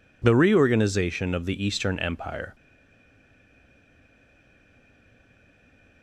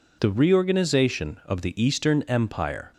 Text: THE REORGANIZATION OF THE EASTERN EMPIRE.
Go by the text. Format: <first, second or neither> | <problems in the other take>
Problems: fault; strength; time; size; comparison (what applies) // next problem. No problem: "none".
second | stays silent after the last word; strong; from 2.5 s on; 3.5 s long